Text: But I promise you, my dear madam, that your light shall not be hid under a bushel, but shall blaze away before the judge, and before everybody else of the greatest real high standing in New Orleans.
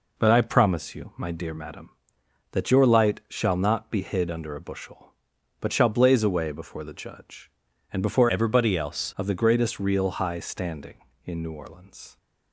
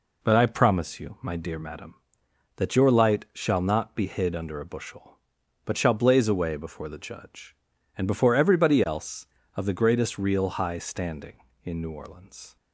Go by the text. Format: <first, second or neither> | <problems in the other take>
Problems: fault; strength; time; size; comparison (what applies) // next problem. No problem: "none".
second | changes voice from "everybody" to "else"; from 8.2 to 9.1 s; 0.9 s long